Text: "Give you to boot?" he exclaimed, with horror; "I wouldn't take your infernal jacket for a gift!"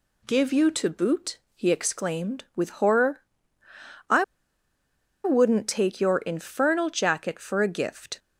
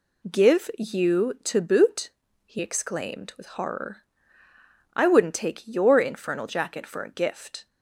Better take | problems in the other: second | pauses between "I" and "wouldn't"; at 4.2 s; 1.0 s long

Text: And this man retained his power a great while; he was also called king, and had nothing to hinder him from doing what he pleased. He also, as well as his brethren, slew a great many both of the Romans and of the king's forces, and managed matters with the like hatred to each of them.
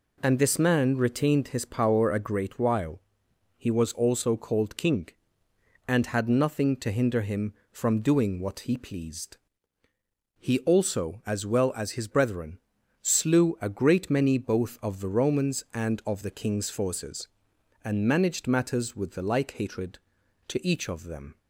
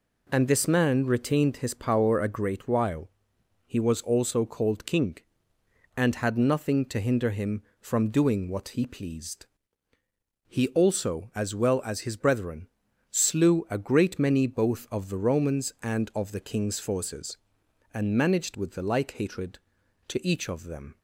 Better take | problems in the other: first | skips "matters"; at 18.5 s

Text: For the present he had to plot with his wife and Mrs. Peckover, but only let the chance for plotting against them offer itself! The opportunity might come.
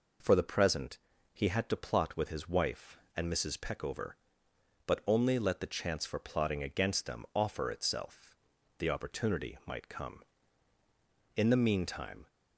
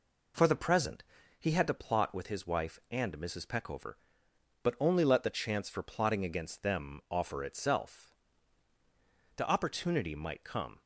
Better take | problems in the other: second | pauses between "present" and "he"; slight; at 0.9 s; 0.34 s long; also in the second // goes on to say "In the meantime"; noticeable; from 11.3 s on; 0.92 s long

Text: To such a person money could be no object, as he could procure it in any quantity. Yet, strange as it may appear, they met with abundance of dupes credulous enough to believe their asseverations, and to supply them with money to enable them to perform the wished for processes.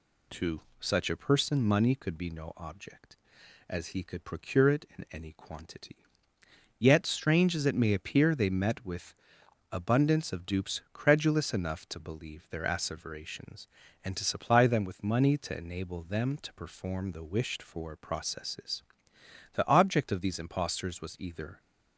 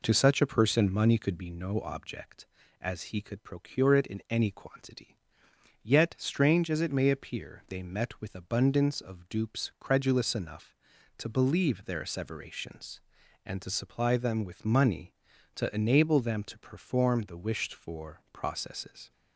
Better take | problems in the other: second | pauses between "To" and "such"; slight; at 0.6 s; 0.18 s long // pauses between "with" and "abundance"; noticeable; at 9.1 s; 0.58 s long // goes on to say "The object of these impostors was either"; strong; from 19.5 s on; 2.0 s long

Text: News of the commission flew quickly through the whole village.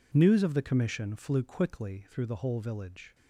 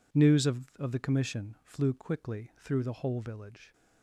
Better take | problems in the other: first | says "of" twice; at 0.7 s

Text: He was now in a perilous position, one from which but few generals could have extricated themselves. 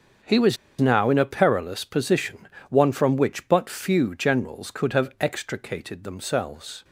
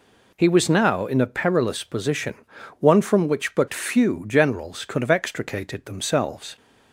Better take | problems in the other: second | starts louder than the rest; until 1.4 s; 7 dB // pauses between "was" and "now"; slight; at 0.5 s; 0.23 s long

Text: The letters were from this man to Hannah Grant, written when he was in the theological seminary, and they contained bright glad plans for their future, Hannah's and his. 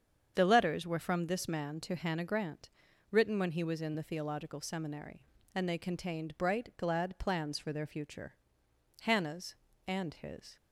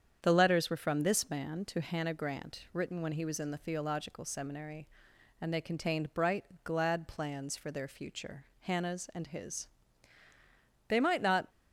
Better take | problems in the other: first | starts louder than the rest; strong; until 1.2 s; 8 dB; strong in the first // pauses between "bright" and "glad"; slight; at 6.4 s; 0.20 s long // goes on to say "They might not"; from 10.8 s on; 0.60 s long

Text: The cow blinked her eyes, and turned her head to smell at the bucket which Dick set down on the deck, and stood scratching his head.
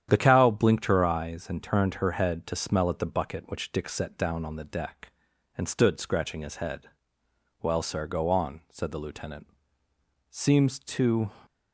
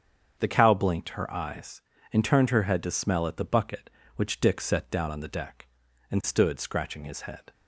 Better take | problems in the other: second | starts louder than the rest; strong; until 1.1 s; 9.5 dB; strong in the second // goes on to say "Well sir go on said the lieutenant Seems to"; strong; from 7.5 s on; 3.7 s long

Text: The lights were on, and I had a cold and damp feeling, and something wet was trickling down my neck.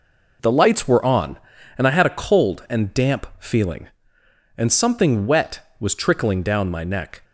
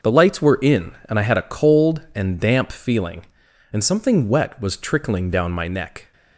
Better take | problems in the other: first | starts louder than the rest; noticeable; until 1.1 s; 6 dB // says "in" for "on"; at 0.5 s

